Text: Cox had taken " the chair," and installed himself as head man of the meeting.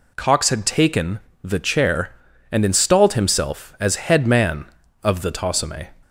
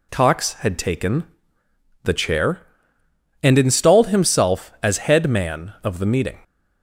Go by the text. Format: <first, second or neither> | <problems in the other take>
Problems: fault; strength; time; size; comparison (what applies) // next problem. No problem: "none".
second | says "tosome" for "meeting"; at 5.3 s